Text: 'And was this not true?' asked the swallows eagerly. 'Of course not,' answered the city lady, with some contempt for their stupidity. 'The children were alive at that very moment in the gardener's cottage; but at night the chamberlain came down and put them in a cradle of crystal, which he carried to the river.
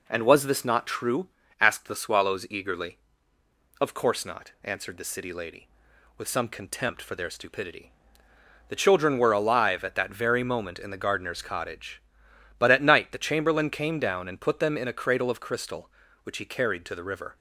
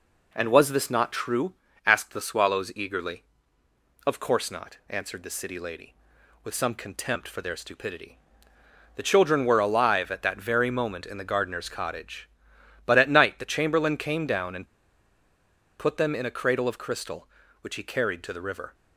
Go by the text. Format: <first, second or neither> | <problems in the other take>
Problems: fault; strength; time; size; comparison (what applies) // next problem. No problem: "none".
first | pauses between "and" and "put"; at 14.6 s; 1.1 s long